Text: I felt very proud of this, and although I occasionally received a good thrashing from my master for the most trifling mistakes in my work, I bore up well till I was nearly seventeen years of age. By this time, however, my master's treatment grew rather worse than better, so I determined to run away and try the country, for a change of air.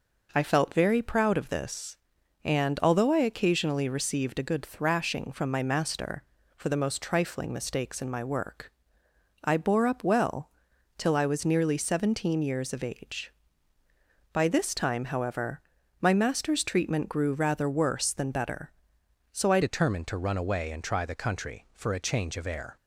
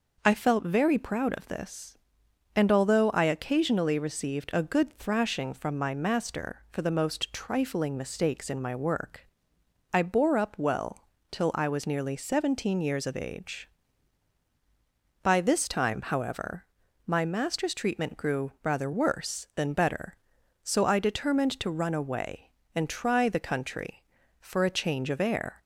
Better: second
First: pauses between "well" and "till"; noticeable; at 10.5 s; 0.48 s long // changes voice at "determined"; from 19.6 s on; 3.1 s long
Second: pauses between "well" and "till"; slight; at 11.0 s; 0.24 s long

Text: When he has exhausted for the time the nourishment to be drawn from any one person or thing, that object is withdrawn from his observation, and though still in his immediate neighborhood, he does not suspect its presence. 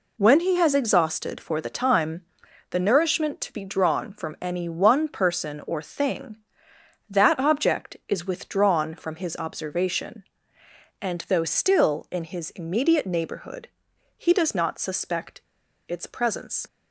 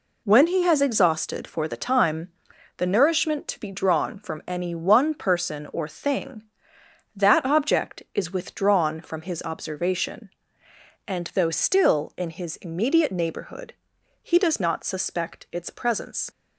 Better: second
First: pauses between "time" and "the"; noticeable; at 2.2 s; 0.48 s long // pauses between "suspect" and "its"; at 15.4 s; 0.45 s long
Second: pauses between "time" and "the"; noticeable; at 2.2 s; 0.48 s long

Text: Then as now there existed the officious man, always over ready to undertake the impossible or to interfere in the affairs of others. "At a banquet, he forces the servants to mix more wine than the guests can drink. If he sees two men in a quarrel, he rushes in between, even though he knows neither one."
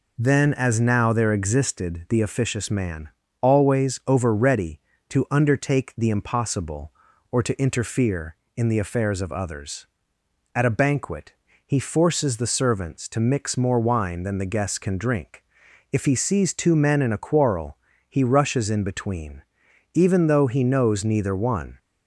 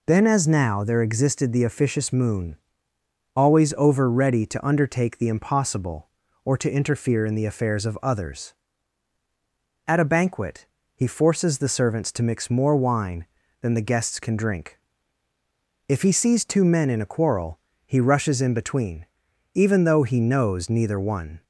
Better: first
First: none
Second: says "moon" for "man"; at 2.1 s

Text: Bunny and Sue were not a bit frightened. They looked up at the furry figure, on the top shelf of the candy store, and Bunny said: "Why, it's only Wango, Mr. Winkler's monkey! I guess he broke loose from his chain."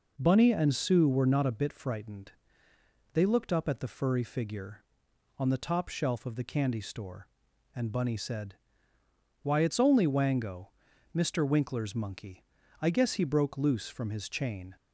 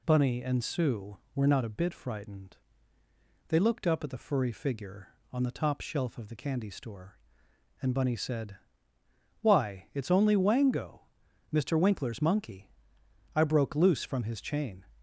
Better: first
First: none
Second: skips "guess he"; at 13.4 s

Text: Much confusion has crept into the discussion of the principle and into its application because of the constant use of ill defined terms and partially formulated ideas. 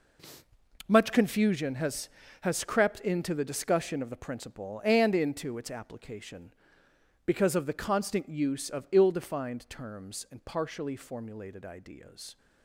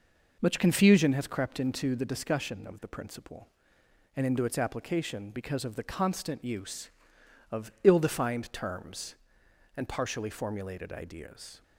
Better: second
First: says "has" twice; at 2.4 s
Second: none

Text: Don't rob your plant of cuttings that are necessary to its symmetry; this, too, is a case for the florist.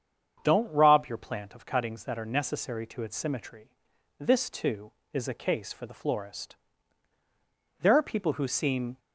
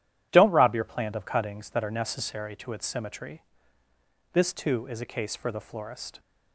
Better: second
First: starts louder than the rest; strong; until 1.4 s; 7.5 dB // goes on to say "There are people who seem"; noticeable; from 7.8 s on; 1.1 s long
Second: none

